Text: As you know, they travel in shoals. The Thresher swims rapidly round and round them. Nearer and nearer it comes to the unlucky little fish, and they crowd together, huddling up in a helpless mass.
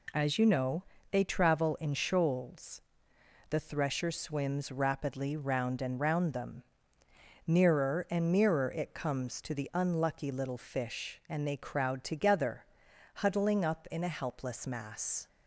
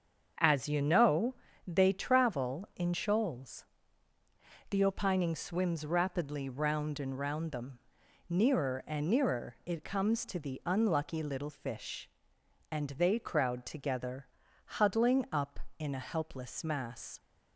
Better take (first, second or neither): first